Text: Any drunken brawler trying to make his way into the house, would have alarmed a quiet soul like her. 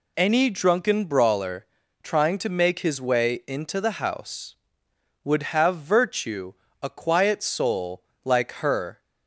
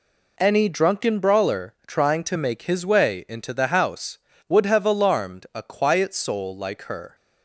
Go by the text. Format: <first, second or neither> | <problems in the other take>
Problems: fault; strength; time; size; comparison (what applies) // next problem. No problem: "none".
second | pauses between "brawler" and "trying"; at 1.6 s; 0.38 s long // says "virtue" for "alarmed"; at 5.7 s // pauses between "soul" and "like"; slight; at 8.0 s; 0.22 s long